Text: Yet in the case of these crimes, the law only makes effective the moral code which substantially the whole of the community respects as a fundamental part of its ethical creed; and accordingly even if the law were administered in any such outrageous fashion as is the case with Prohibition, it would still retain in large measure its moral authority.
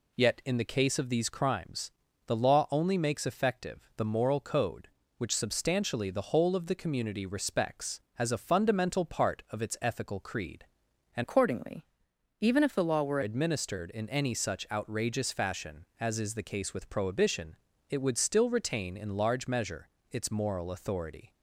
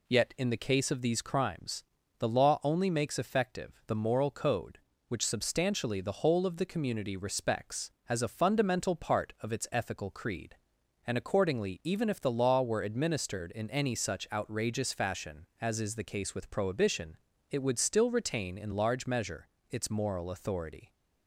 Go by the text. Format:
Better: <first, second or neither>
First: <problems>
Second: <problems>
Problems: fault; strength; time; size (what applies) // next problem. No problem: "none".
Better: second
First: changes voice from "accordingly" to "were"; from 11.2 to 13.2 s; 2.0 s long // pauses between "accordingly" and "even"; noticeable; at 11.8 s; 0.54 s long // pauses between "measure" and "its"; slight; at 19.8 s; 0.22 s long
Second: pauses between "measure" and "its"; slight; at 19.4 s; 0.22 s long